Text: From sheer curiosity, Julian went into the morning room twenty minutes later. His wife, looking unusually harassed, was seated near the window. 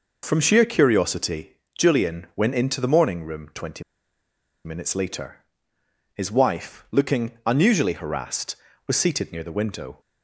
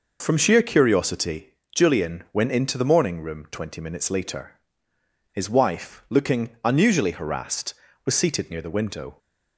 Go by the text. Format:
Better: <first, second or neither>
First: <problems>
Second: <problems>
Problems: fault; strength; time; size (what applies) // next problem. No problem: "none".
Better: second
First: pauses between "twenty" and "minutes"; noticeable; at 3.8 s; 0.82 s long // pauses between "looking" and "unusually"; slight; at 7.2 s; 0.16 s long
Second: pauses between "looking" and "unusually"; slight; at 6.4 s; 0.16 s long